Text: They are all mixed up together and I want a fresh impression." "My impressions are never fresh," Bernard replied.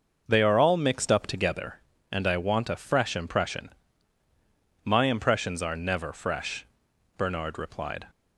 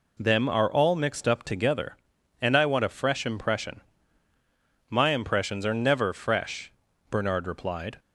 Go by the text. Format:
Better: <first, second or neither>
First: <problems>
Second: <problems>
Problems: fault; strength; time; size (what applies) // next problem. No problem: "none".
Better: first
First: none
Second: says "Them" for "They"; at 0.1 s